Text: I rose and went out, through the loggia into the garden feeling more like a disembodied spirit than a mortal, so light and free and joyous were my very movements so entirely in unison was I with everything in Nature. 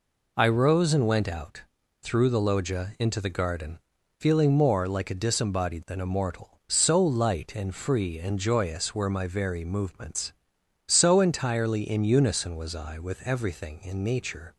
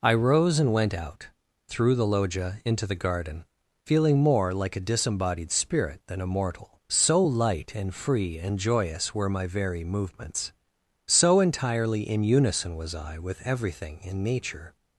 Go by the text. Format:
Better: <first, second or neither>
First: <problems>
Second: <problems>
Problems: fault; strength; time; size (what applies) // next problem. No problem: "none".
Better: second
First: pauses between "garden" and "feeling"; at 3.7 s; 0.38 s long // skips "spirit"; at 5.8 s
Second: pauses between "garden" and "feeling"; at 3.4 s; 0.38 s long